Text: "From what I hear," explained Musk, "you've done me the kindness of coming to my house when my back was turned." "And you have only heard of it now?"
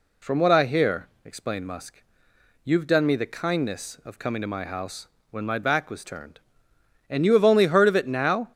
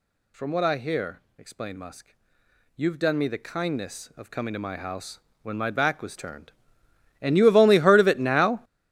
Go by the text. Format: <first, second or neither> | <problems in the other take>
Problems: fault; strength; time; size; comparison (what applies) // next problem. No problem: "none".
first | gets louder; strong; throughout; 15 dB // pauses between "house" and "when"; slight; at 5.1 s; 0.24 s long; slight in the first